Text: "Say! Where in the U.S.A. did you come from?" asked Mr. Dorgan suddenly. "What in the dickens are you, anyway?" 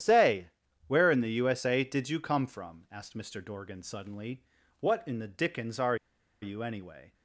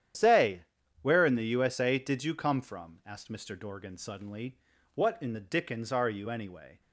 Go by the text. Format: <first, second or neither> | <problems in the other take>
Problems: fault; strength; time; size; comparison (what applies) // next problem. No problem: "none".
second | starts louder than the rest; strong; until 1.4 s; 10 dB; strong in the second // pauses between "are" and "you"; noticeable; at 5.9 s; 0.46 s long